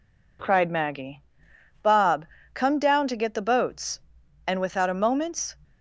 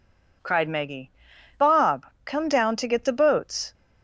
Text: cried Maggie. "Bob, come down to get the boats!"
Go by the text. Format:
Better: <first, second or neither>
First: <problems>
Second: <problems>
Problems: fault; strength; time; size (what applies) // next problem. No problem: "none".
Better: second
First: goes on to say "And without a moment's"; noticeable; from 4.4 s on; 1.0 s long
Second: none